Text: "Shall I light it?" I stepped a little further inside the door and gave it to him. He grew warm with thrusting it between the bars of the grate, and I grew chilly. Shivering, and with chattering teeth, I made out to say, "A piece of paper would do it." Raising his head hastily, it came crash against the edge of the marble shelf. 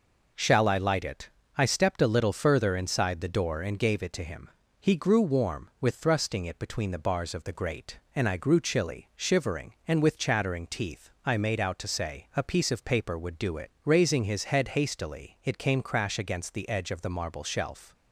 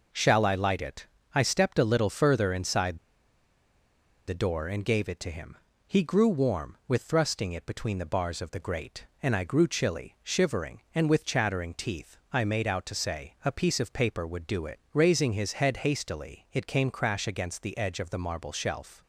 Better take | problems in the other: first | pauses between "inside" and "the"; strong; at 2.9 s; 1.3 s long

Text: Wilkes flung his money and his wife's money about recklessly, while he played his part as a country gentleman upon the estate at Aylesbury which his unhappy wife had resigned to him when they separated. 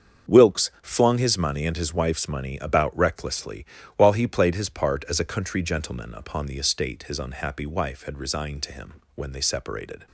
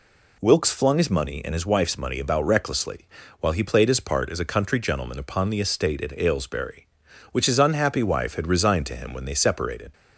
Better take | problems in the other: second | starts louder than the rest; until 1.3 s; 7 dB // skips "at Aylesbury which"; at 7.0 s // pauses between "him" and "when"; slight; at 8.9 s; 0.20 s long

